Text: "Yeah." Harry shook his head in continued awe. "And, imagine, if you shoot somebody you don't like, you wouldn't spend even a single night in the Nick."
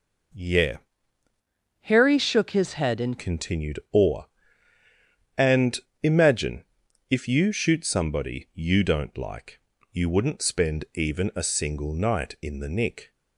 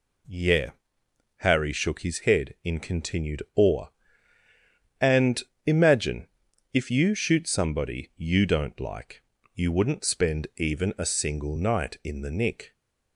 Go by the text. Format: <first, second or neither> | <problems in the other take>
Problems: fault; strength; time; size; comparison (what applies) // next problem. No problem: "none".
second | changes voice from "Harry" to "in"; from 1.8 to 3.1 s; 1.3 s long